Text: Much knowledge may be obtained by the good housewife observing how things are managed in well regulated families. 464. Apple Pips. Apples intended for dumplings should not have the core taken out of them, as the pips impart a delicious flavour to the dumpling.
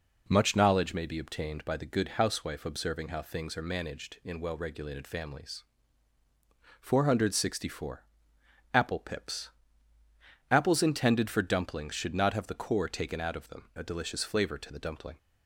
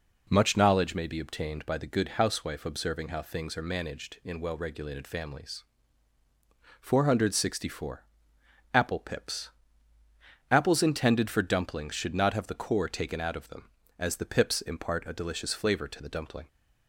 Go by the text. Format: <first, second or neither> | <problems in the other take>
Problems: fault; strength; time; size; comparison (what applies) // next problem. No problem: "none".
second | skips "as the pips impart"; at 13.7 s